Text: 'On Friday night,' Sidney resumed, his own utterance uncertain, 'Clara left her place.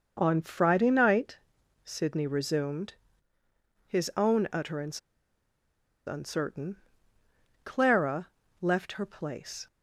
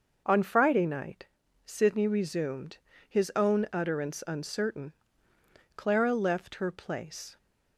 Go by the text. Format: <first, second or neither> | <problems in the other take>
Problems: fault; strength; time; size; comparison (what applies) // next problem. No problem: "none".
second | starts louder than the rest; noticeable; until 1.2 s; 6 dB // pauses between "utterance" and "uncertain"; at 4.9 s; 1.0 s long // pauses between "Clara" and "left"; slight; at 8.2 s; 0.32 s long